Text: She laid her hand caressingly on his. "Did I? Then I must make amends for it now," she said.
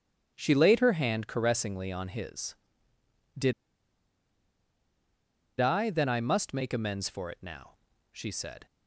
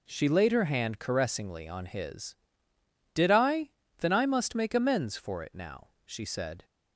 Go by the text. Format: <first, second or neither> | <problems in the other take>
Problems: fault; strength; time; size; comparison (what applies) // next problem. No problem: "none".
second | starts louder than the rest; strong; until 1.3 s; 8.5 dB // pauses between "Did" and "I"; strong; at 3.5 s; 2.0 s long